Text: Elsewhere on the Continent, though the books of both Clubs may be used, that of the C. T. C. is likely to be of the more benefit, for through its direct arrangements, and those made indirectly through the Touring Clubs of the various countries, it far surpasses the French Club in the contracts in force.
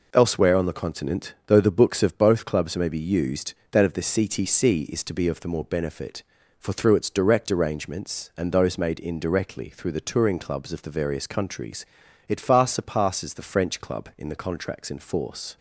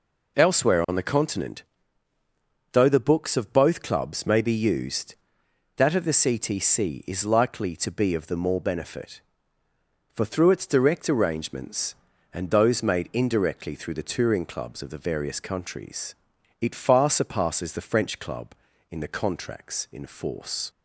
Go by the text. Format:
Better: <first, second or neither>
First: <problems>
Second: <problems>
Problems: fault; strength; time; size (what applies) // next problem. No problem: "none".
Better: second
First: skips "likely"; at 5.0 s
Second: none